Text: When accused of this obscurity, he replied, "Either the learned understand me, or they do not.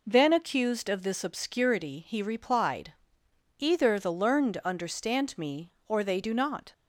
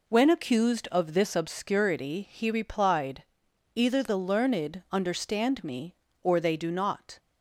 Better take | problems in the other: second | says "Then" for "When"; at 0.0 s

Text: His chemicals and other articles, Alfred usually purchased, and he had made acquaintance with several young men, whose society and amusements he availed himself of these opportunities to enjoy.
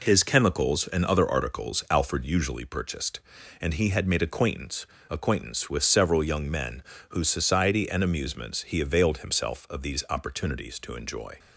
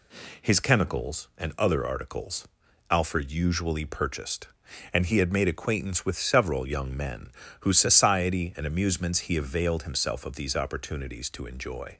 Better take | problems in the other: second | says "acquaintance" twice; at 5.0 s

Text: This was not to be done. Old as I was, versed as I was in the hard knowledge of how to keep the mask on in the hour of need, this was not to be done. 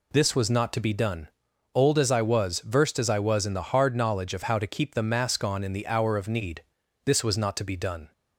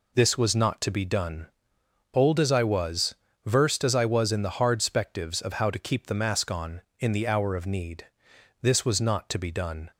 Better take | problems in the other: first | says "spectives" for "knowledge"; at 4.8 s

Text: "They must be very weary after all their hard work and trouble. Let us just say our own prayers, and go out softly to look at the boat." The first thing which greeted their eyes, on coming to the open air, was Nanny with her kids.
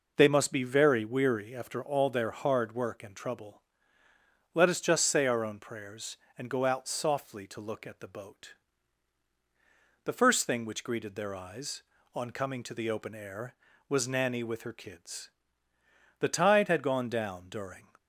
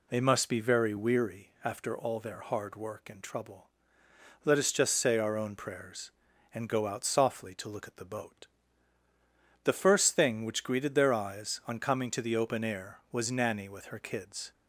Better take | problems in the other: second | goes on to say "The tide had gone down during"; strong; from 16.1 s on; 1.7 s long

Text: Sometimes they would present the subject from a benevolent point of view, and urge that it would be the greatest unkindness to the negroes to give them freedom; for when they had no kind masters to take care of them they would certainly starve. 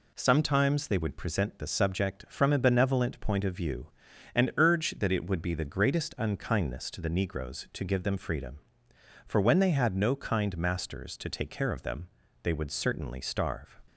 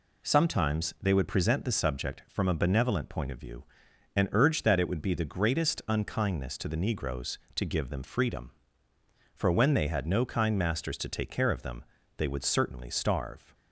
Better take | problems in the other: neither | pauses between "them" and "they"; slight; the same in both

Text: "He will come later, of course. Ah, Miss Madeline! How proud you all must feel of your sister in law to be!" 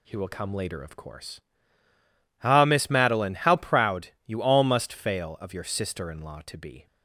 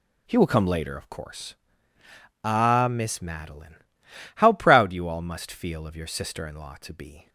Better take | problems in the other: second | says "fail" for "feel"; at 4.9 s

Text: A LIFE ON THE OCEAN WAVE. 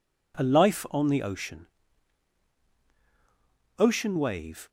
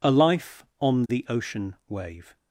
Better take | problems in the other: second | says "OCEAN" twice; at 3.7 s

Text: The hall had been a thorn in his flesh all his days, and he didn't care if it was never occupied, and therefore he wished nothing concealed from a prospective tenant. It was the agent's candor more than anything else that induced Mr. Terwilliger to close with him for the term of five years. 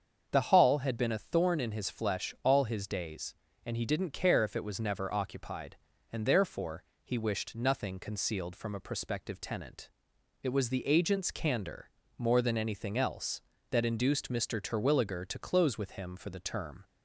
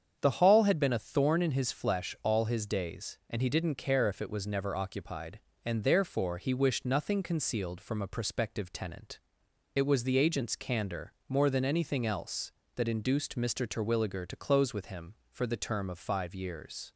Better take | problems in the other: second | starts louder than the rest; until 1.3 s; 7 dB; strong in the second // pauses between "therefore" and "he"; slight; at 6.8 s; 0.18 s long // pauses between "candor" and "more"; slight; at 11.8 s; 0.28 s long; slight in the second // stops before "of five years"; at 16.8 s

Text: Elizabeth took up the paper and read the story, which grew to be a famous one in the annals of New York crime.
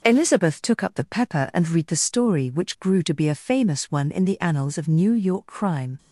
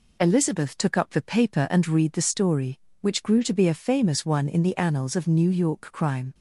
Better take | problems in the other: second | says "pepper" for "paper"; at 1.0 s

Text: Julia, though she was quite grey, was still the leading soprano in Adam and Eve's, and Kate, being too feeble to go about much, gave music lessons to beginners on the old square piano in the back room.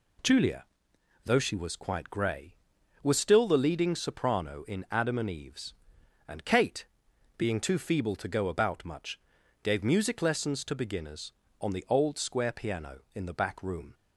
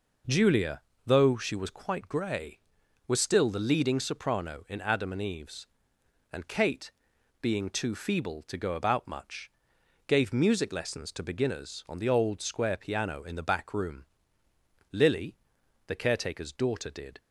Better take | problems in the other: first | goes on to say "Lily the caretaker's daughter did"; strong; from 14.9 s on; 2.2 s long

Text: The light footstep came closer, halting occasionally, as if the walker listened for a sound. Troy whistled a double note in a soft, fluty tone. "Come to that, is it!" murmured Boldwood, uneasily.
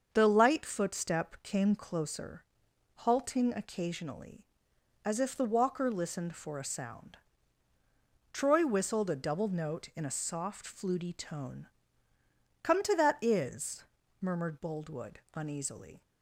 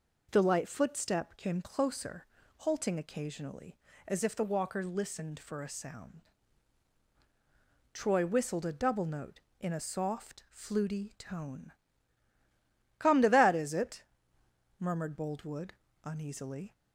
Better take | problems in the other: second | starts louder than the rest; until 1.1 s; 6.5 dB // skips "it"; at 14.0 s

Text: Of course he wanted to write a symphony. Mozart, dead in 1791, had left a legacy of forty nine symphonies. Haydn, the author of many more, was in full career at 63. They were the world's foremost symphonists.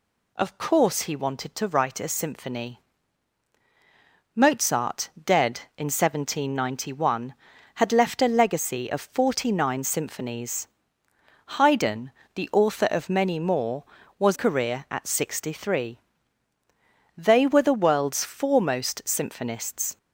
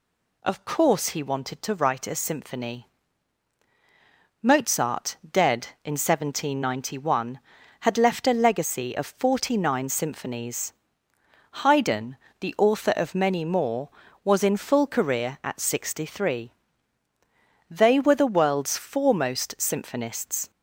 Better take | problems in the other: second | skips "in full"; at 14.3 s

